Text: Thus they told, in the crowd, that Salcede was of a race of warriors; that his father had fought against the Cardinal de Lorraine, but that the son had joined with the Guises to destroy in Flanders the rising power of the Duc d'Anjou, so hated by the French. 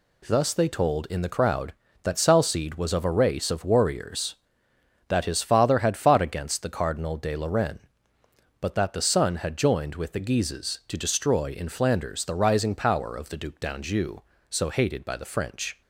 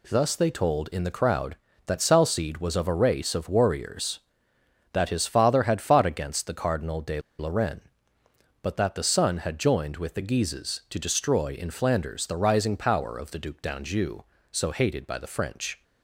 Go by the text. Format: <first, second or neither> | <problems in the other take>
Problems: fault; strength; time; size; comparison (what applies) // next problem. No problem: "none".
first | pauses between "de" and "Lorraine"; slight; at 7.1 s; 0.19 s long